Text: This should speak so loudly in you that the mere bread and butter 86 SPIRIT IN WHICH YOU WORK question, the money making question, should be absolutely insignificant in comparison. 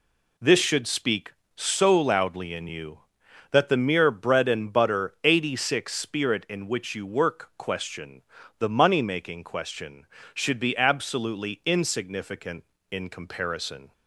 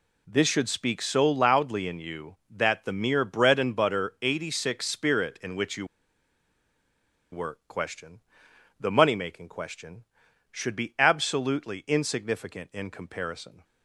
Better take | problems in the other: first | pauses between "YOU" and "WORK"; strong; at 5.8 s; 1.4 s long

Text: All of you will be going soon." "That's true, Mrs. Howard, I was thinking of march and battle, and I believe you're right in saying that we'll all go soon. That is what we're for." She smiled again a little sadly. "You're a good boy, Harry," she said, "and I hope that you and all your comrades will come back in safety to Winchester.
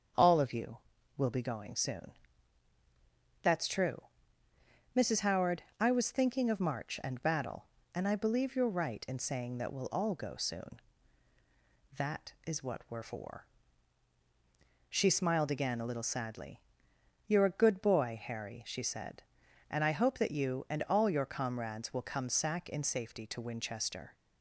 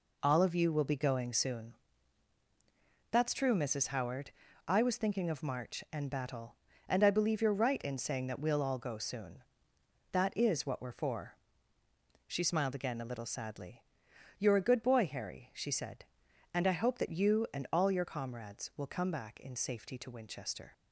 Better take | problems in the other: second | starts louder than the rest; strong; until 1.5 s; 7.5 dB // says "sack" for "back"; at 22.2 s

